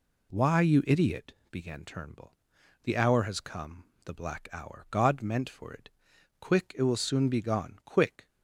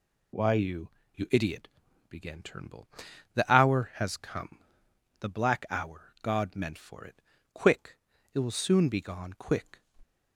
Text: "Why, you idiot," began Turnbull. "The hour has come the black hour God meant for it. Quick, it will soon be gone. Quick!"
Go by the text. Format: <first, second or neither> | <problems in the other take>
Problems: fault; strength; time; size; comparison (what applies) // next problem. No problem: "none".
first | says "you" twice; at 1.1 s // pauses between "come" and "the"; noticeable; at 4.5 s; 0.62 s long; slight in the first